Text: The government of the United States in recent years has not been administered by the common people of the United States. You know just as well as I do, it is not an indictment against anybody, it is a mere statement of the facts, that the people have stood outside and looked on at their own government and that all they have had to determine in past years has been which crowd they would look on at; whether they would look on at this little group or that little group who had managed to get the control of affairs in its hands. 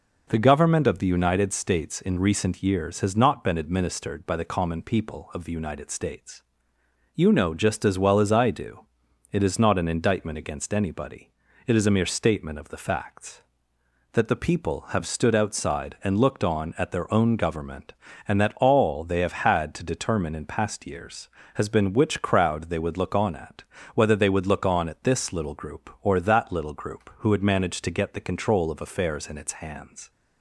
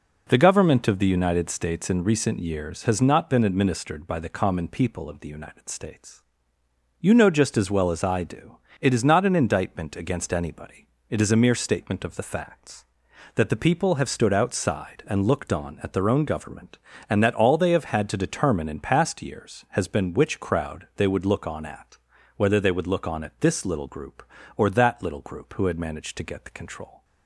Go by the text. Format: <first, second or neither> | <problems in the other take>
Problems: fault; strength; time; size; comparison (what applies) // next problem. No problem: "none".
first | stops before "of affairs in its hands"; at 27.0 s